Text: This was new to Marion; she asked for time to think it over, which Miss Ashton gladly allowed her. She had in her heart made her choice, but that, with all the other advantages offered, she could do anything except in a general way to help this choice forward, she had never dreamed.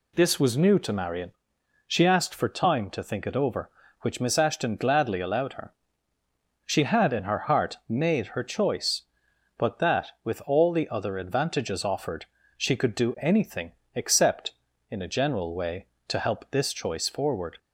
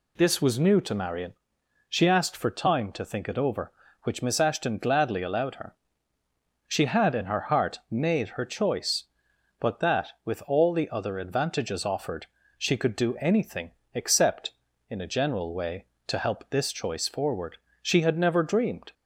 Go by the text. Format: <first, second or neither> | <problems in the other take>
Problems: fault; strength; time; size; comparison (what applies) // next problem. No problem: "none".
second | pauses between "anything" and "except"; slight; at 13.7 s; 0.22 s long; slight in the second // stops before "she had never dreamed"; at 17.5 s